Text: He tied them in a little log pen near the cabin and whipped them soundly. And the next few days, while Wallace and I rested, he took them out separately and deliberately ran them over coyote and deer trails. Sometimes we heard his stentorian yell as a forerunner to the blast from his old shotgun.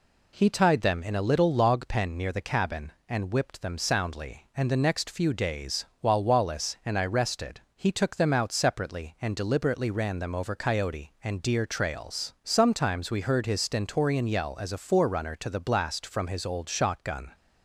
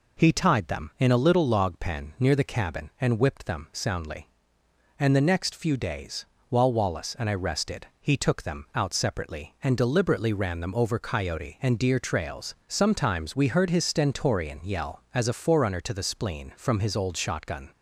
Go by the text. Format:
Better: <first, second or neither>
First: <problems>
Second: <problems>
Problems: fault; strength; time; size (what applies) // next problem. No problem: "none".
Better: first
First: none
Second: says "spleen" for "blast"; at 16.0 s